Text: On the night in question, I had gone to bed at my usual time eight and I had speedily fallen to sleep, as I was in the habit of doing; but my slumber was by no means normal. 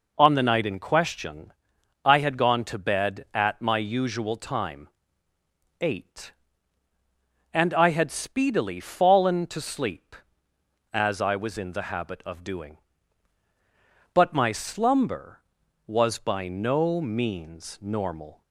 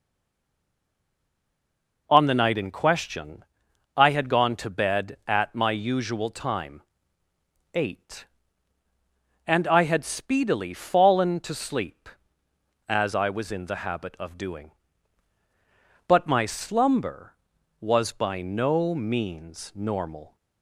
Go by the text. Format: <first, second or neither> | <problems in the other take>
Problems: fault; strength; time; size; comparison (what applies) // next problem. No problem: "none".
first | stays silent before the first word; noticeable; until 2.0 s; 2.0 s long // pauses between "time" and "eight"; noticeable; at 6.8 s; 0.92 s long; noticeable in the first